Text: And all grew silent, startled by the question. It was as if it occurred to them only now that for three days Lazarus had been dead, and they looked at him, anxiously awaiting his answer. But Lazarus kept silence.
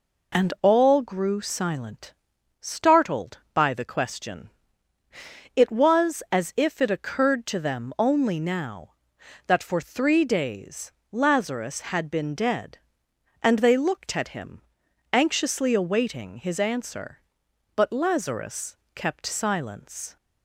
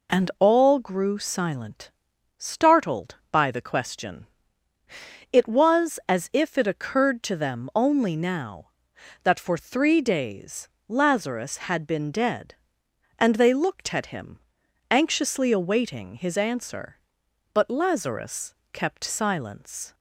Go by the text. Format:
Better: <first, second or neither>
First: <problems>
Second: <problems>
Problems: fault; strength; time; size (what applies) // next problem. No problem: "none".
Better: neither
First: pauses between "days" and "Lazarus"; slight; at 10.9 s; 0.20 s long // pauses between "Lazarus" and "kept"; slight; at 18.7 s; 0.18 s long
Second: pauses between "days" and "Lazarus"; slight; at 10.6 s; 0.20 s long // pauses between "Lazarus" and "kept"; slight; at 18.5 s; 0.18 s long